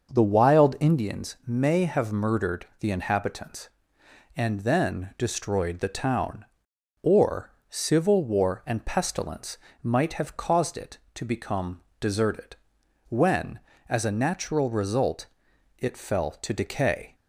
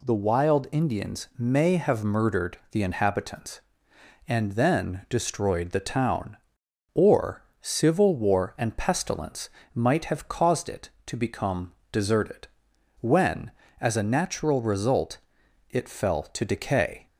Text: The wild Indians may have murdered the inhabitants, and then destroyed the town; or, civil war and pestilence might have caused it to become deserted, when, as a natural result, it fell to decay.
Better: second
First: starts louder than the rest; until 1.1 s; 6 dB // pauses between "pestilence" and "might"; slight; at 9.5 s; 0.24 s long // pauses between "become" and "deserted"; slight; at 11.8 s; 0.20 s long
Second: pauses between "pestilence" and "might"; slight; at 9.5 s; 0.24 s long // pauses between "become" and "deserted"; slight; at 11.7 s; 0.20 s long

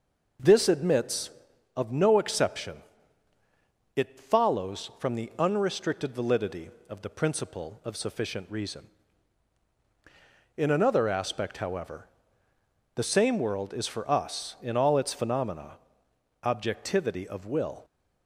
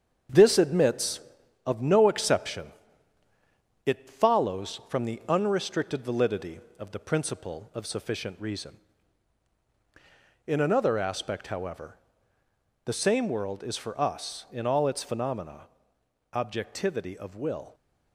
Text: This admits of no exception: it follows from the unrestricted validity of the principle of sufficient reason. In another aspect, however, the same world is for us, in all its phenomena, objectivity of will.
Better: first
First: none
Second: gets quieter; noticeable; throughout; 5.5 dB

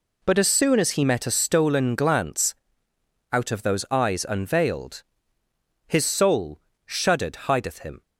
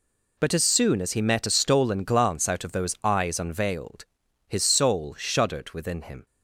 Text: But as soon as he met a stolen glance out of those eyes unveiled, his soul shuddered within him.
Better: second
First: pauses between "glance" and "out"; noticeable; at 2.5 s; 0.78 s long // pauses between "soul" and "shuddered"; slight; at 6.5 s; 0.26 s long // says "hideth" for "within"; at 7.3 s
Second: none

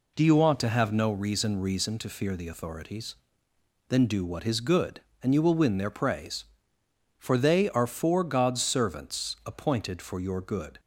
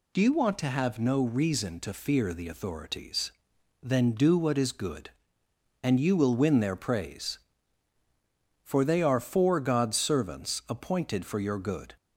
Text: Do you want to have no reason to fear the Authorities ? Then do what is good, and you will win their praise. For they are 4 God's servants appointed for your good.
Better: second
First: says "reason" twice; at 1.5 s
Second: none

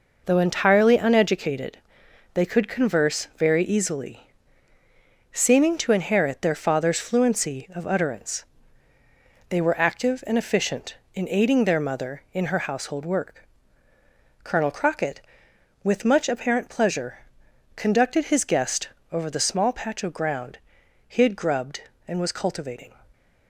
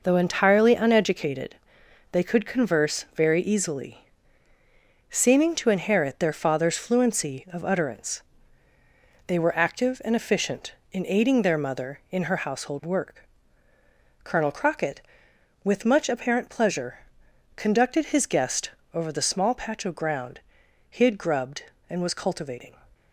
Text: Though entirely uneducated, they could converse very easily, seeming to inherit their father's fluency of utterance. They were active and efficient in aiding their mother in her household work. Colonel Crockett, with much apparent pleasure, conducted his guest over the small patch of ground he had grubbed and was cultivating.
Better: neither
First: pauses between "guest" and "over"; slight; at 18.8 s; 0.22 s long // pauses between "ground" and "he"; noticeable; at 20.5 s; 0.50 s long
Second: pauses between "guest" and "over"; slight; at 18.7 s; 0.22 s long // pauses between "ground" and "he"; noticeable; at 20.4 s; 0.50 s long

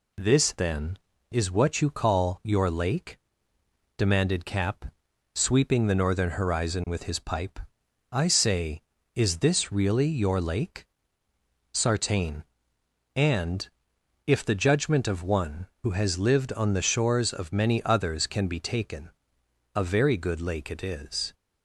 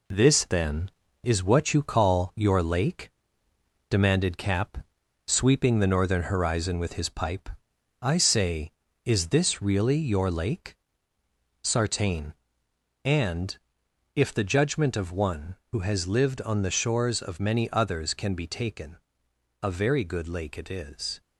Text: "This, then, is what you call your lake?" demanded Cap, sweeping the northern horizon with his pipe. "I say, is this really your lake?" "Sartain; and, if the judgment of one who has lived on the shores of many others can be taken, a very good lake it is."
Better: first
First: none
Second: gets quieter; noticeable; throughout; 5 dB

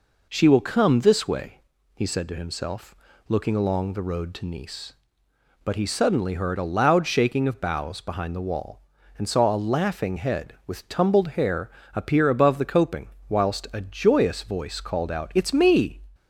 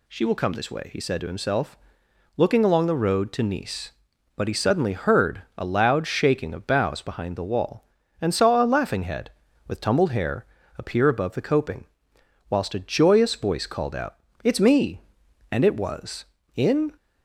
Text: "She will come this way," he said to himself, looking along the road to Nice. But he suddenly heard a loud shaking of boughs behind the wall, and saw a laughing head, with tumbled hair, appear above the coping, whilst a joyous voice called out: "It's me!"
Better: first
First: none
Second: goes on to say "And it was in"; from 15.5 s on; 1.4 s long

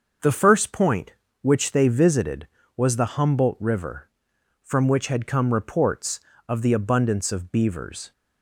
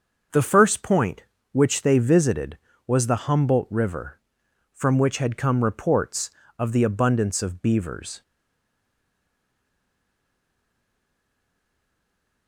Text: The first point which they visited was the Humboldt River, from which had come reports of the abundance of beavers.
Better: first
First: starts louder than the rest; until 1.4 s; 6 dB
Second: starts louder than the rest; until 1.5 s; 6 dB // stays silent after the last word; strong; from 8.2 s on; 4.2 s long

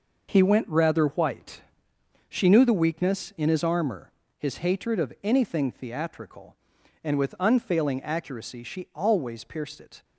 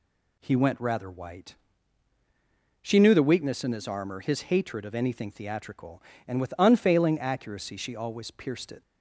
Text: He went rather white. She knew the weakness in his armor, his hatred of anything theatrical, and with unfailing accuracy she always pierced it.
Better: second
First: gets quieter; strong; throughout; 8 dB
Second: none

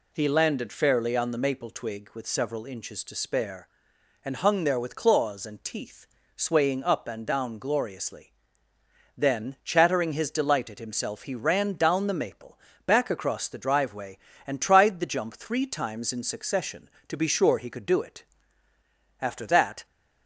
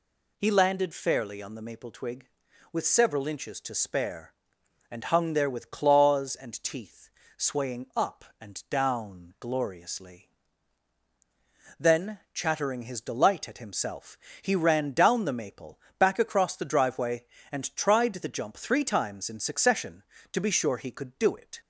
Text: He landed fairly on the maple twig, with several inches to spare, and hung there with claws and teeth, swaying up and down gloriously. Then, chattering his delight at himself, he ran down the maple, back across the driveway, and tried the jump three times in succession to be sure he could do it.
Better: second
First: goes on to say "After that"; noticeable; from 19.2 s on; 0.64 s long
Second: none

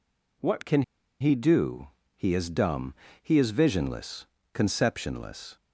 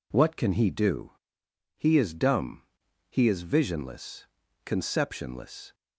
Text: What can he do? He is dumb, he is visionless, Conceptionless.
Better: second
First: pauses between "can" and "he"; at 0.8 s; 0.38 s long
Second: none

